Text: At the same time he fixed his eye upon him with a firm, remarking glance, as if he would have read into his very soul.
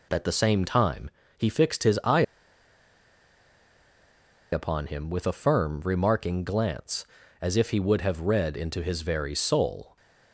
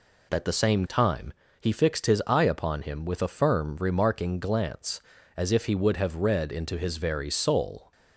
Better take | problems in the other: second | pauses between "time" and "he"; slight; at 1.1 s; 0.26 s long; slight in the second // pauses between "eye" and "upon"; strong; at 2.2 s; 2.2 s long

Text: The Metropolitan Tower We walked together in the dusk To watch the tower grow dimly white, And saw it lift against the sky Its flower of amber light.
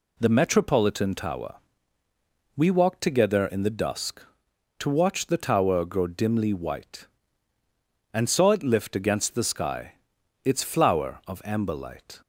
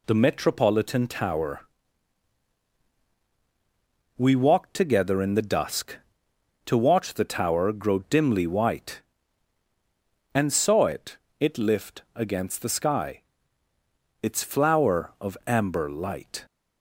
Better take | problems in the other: first | pauses between "Tower" and "We"; strong; at 1.6 s; 2.5 s long; noticeable in the first // says "it" twice; at 11.4 s // pauses between "sky" and "Its"; at 13.2 s; 1.0 s long; noticeable in the first

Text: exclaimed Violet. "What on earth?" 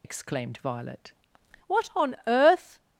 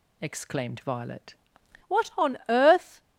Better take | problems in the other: second | loses the start of "exclaimed"; at 0.0 s; 60 ms

